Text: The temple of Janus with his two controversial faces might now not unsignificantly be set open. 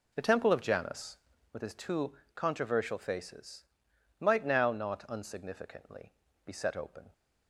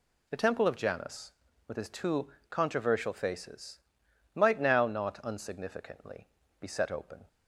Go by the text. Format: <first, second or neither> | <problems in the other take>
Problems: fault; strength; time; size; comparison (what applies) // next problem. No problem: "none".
second | starts louder than the rest; noticeable; until 1.6 s; 4.5 dB // pauses between "two" and "controversial"; slight; at 2.1 s; 0.22 s long; slight in the second // pauses between "faces" and "might"; noticeable; at 3.6 s; 0.56 s long; noticeable in the second // pauses between "unsignificantly" and "be"; slight; at 6.1 s; 0.32 s long; slight in the second